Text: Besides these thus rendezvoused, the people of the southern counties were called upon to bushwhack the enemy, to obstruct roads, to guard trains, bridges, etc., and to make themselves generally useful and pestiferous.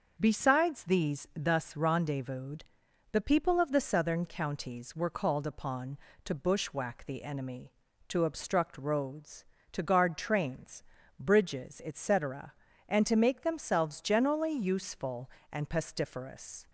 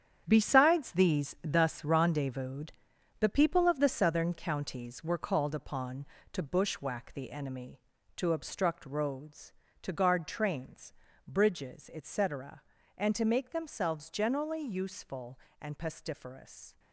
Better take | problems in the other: first | gets quieter; strong; throughout; 10 dB // starts louder than the rest; strong; until 1.2 s; 8.5 dB; also in the first

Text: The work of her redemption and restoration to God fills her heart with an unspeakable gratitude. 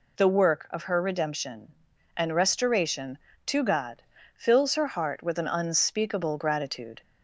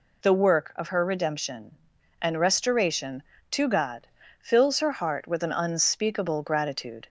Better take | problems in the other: neither | pauses between "God" and "fills"; slight; the same in both

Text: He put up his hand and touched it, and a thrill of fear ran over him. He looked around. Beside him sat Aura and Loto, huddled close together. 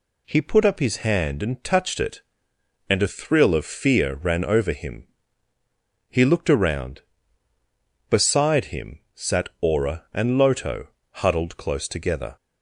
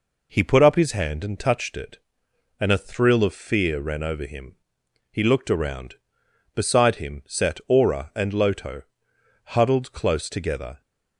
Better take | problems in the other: neither | none

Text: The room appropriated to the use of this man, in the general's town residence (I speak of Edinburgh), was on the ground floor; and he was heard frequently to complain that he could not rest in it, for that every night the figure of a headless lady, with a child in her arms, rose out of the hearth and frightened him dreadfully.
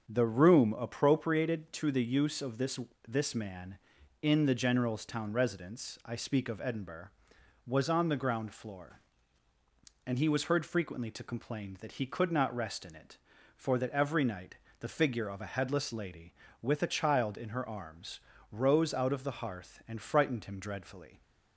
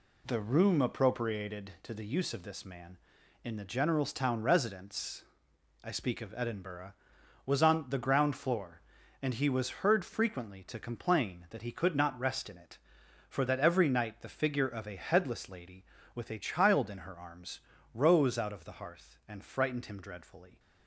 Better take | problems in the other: second | starts louder than the rest; until 1.1 s; 7 dB // says "this" twice; at 3.0 s // pauses between "night" and "the"; slight; at 14.5 s; 0.22 s long

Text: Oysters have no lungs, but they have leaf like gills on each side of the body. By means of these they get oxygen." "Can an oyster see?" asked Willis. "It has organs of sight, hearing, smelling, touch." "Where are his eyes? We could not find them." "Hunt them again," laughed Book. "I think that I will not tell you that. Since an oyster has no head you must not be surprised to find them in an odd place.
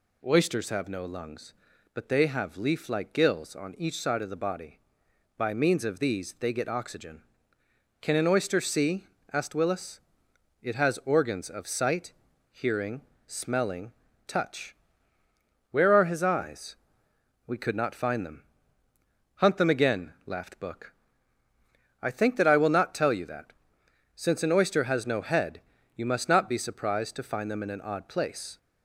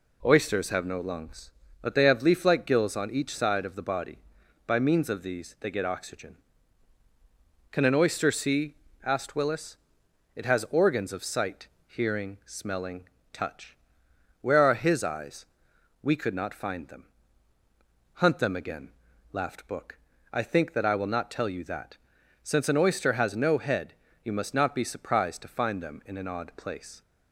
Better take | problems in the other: neither | pauses between "head" and "you"; slight; the same in both

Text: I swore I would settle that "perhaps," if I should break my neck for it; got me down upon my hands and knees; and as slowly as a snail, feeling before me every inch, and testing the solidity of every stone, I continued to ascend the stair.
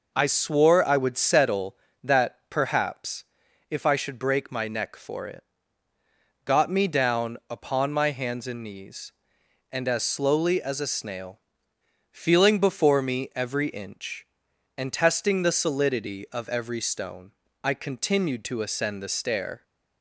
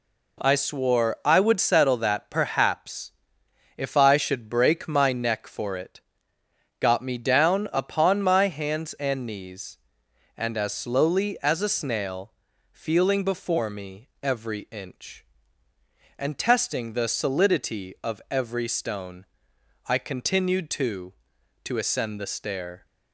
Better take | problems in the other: first | pauses between "me" and "every"; slight; at 14.0 s; 0.16 s long // says "to" twice; at 21.6 s

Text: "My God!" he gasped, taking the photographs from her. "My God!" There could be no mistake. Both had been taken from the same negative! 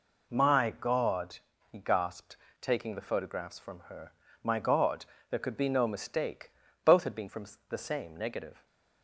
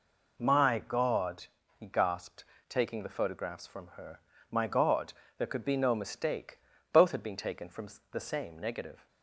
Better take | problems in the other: second | skips "taken"; at 7.2 s // pauses between "from" and "the"; slight; at 7.4 s; 0.24 s long; slight in the second // stays silent after the last word; slight; from 8.5 s on; 0.5 s long

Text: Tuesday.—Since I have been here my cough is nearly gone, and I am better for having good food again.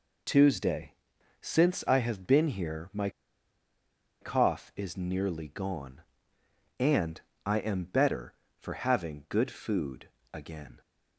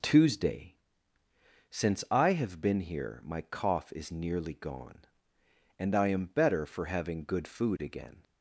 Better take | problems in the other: second | pauses between "my" and "cough"; at 3.0 s; 1.1 s long // pauses between "and" and "I"; slight; at 7.1 s; 0.24 s long // pauses between "food" and "again"; slight; at 10.0 s; 0.22 s long

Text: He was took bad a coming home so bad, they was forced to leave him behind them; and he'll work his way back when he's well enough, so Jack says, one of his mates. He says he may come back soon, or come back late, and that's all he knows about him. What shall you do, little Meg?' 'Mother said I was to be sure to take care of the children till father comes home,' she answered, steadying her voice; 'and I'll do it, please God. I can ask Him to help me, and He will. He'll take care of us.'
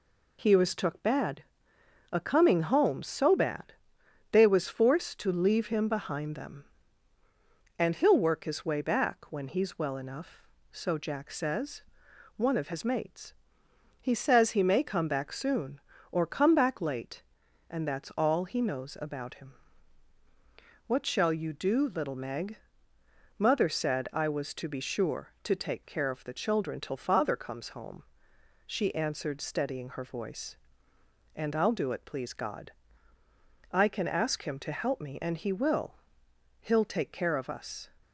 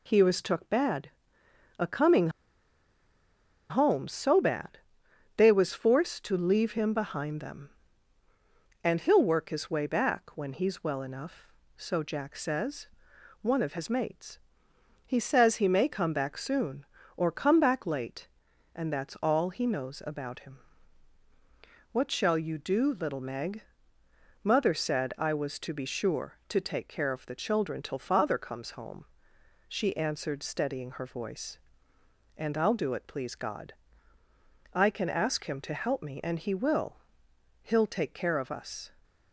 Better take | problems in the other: first | pauses between "bad" and "a"; noticeable; at 1.0 s; 0.72 s long; noticeable in the first // pauses between "coming" and "home"; strong; at 2.2 s; 1.4 s long

